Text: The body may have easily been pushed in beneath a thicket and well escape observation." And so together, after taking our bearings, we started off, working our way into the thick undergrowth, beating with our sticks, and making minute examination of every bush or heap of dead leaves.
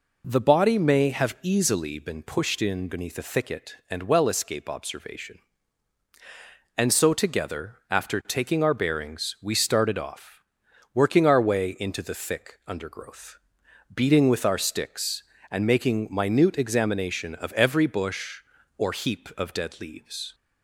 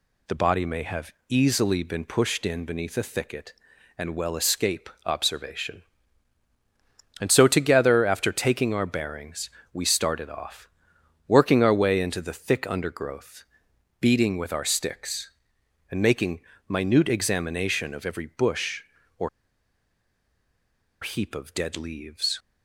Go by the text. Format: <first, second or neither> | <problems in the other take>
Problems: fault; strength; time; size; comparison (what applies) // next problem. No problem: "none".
first | pauses between "have" and "easily"; slight; at 1.1 s; 0.16 s long // pauses between "escape" and "observation"; slight; at 4.8 s; 0.16 s long // pauses between "making" and "minute"; slight; at 16.4 s; 0.28 s long // pauses between "or" and "heap"; strong; at 19.2 s; 1.7 s long